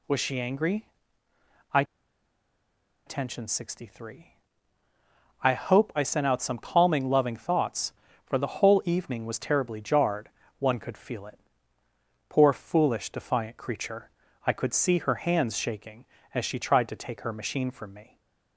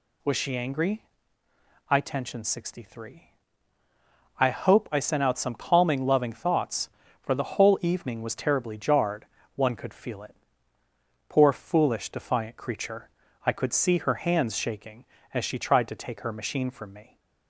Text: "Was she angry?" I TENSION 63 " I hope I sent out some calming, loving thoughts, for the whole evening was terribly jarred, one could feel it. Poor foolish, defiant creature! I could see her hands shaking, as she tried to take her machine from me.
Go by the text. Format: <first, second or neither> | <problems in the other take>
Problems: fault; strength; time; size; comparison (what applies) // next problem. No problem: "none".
second | pauses between "I" and "TENSION"; at 1.8 s; 1.2 s long // stays silent after the last word; slight; from 18.0 s on; 0.5 s long